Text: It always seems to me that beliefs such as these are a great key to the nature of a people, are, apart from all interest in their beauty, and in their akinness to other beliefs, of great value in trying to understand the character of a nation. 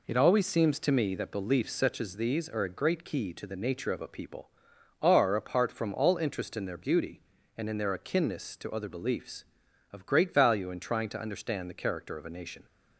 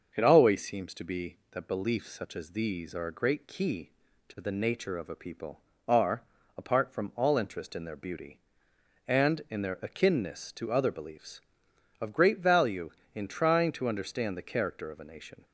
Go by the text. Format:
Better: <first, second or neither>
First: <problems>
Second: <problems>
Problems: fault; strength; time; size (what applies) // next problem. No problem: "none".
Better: first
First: none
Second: starts louder than the rest; noticeable; until 1.1 s; 6 dB // says "be" for "me"; at 1.0 s